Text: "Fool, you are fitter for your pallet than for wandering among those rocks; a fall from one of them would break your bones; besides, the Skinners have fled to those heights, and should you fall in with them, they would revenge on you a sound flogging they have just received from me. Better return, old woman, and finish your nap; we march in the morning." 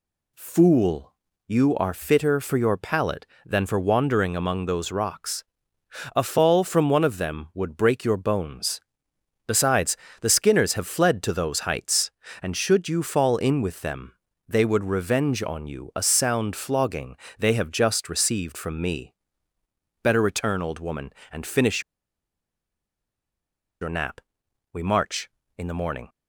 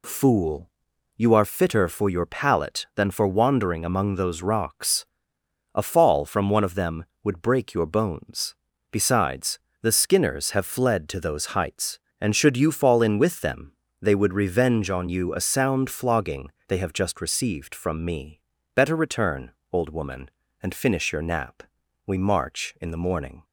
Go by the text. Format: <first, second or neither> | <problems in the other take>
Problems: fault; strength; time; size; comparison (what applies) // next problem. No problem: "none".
second | pauses between "flogging" and "they"; slight; at 17.1 s; 0.22 s long; slight in the second // pauses between "finish" and "your"; strong; at 21.8 s; 2.0 s long